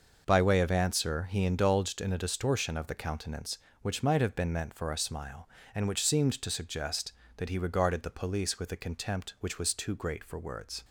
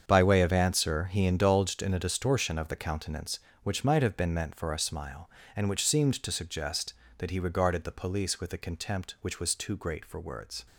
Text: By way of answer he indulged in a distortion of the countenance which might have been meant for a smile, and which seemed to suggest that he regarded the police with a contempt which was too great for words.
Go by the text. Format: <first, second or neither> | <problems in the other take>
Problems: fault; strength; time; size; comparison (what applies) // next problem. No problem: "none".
first | gets quieter; strong; throughout; 12.5 dB